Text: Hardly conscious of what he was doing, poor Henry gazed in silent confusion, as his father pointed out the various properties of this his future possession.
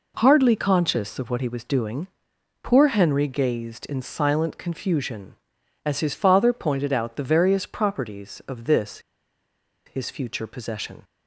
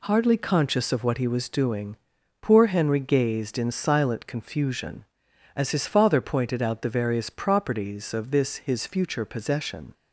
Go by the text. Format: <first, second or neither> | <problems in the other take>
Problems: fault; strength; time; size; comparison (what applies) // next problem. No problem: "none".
second | pauses between "this" and "his"; noticeable; at 8.9 s; 0.86 s long